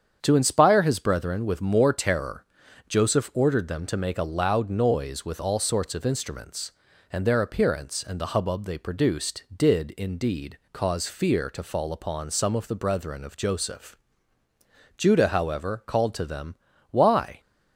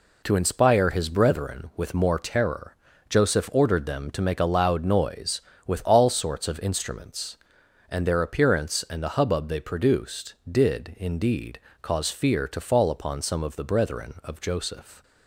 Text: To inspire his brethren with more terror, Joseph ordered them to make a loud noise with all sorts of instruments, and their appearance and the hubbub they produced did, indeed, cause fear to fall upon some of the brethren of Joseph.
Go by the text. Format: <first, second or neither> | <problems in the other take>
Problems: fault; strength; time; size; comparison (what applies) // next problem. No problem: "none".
second | starts louder than the rest; strong; until 1.2 s; 8 dB // goes on to say "Judah however called to them Why"; strong; from 14.9 s on; 2.4 s long